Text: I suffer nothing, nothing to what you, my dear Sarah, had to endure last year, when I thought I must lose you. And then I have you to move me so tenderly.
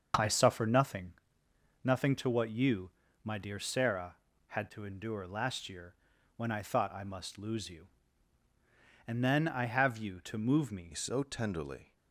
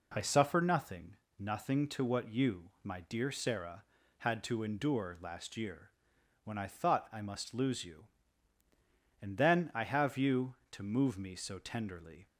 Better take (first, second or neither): second